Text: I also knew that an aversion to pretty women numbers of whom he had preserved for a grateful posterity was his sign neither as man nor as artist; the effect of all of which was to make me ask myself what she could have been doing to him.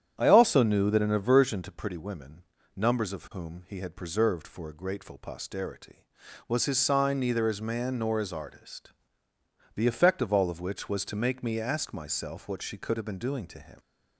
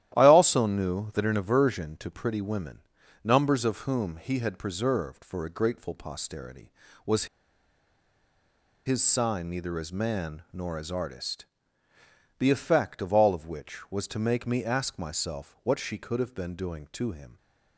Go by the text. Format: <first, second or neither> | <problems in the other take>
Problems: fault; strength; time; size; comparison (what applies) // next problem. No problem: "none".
first | starts louder than the rest; strong; until 1.1 s; 12.5 dB; strong in the first // pauses between "women" and "numbers"; at 2.7 s; 0.44 s long; slight in the first // pauses between "was" and "his"; strong; at 7.2 s; 1.6 s long